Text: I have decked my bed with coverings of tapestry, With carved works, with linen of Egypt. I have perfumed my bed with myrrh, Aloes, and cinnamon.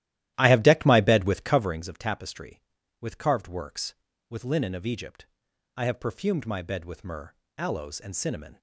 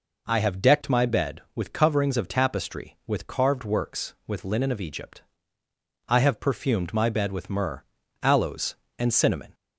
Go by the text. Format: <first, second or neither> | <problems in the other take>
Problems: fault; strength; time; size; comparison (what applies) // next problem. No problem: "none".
second | starts louder than the rest; strong; until 1.8 s; 14 dB